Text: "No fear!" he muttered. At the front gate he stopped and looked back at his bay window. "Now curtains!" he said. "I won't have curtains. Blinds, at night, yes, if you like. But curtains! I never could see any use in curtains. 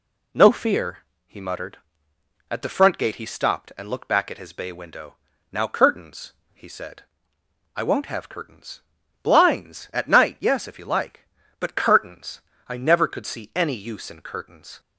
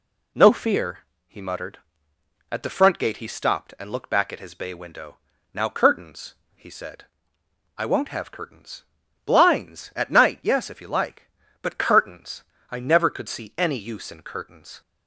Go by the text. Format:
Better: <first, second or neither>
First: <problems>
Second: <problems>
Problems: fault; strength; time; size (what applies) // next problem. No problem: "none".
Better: neither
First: none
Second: none